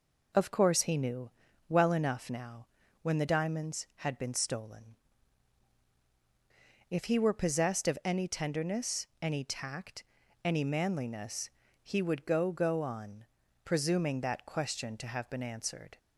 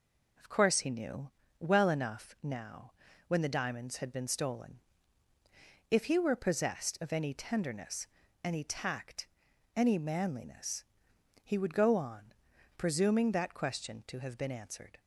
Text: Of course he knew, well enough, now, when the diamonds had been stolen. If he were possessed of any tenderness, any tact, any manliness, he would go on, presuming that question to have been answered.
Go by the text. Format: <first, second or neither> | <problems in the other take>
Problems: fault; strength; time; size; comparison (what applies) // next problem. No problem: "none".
second | says "go" twice; at 12.5 s